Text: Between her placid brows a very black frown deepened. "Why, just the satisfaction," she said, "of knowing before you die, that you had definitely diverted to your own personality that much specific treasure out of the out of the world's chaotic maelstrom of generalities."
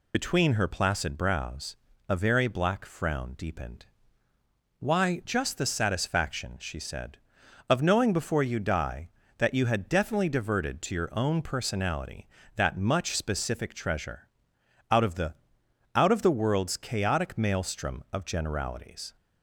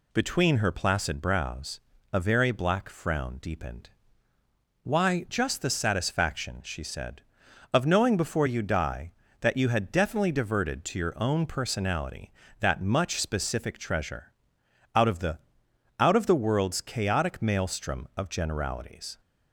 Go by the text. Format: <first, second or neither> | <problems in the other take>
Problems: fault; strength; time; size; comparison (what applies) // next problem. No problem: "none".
second | loses the start of "Between"; at 0.1 s; 60 ms // pauses between "brows" and "a"; slight; at 1.7 s; 0.34 s long; slight in the second // pauses between "treasure" and "out"; noticeable; at 14.2 s; 0.64 s long; noticeable in the second // pauses between "the" and "out"; noticeable; at 15.3 s; 0.62 s long; noticeable in the second